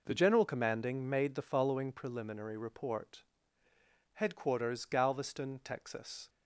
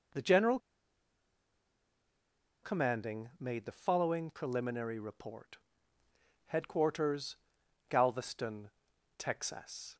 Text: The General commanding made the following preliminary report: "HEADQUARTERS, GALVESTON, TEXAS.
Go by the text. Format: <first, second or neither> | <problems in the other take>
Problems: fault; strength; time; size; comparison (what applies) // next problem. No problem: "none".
first | pauses between "General" and "commanding"; strong; at 0.5 s; 2.0 s long